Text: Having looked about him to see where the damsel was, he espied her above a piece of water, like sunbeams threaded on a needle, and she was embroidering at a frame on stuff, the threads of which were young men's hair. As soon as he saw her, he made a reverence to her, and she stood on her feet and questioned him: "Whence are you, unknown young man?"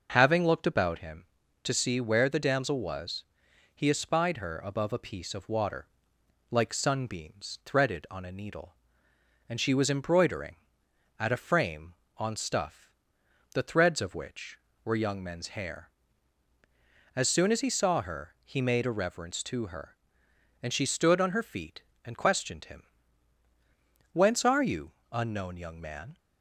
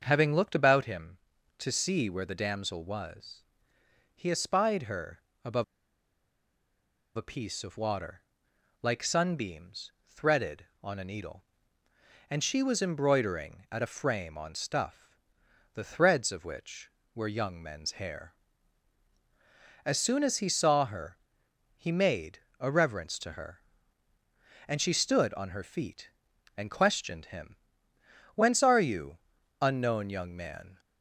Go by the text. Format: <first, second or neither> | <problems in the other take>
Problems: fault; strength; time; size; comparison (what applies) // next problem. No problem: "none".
first | starts louder than the rest; until 1.0 s; 6.5 dB // pauses between "her" and "above"; slight; at 5.2 s; 0.24 s long // pauses between "above" and "a"; strong; at 5.6 s; 1.5 s long // pauses between "sunbeams" and "threaded"; slight; at 9.9 s; 0.18 s long // pauses between "made" and "a"; slight; at 22.3 s; 0.20 s long